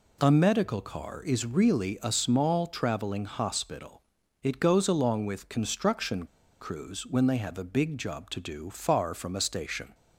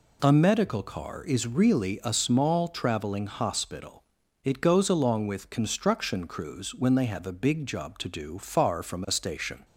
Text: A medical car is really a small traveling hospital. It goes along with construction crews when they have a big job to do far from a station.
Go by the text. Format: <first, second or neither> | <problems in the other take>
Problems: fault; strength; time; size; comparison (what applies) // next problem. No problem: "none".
second | pauses between "construction" and "crews"; slight; at 6.2 s; 0.35 s long